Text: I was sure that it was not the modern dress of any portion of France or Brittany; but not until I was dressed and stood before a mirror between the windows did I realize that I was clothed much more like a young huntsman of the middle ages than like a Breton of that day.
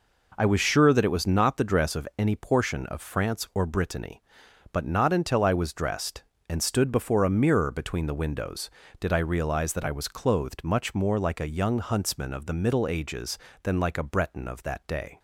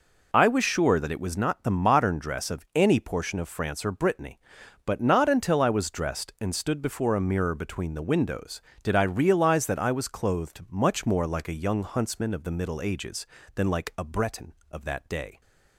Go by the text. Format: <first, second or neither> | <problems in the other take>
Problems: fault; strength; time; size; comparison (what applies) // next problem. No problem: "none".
second | skips "modern"; at 1.6 s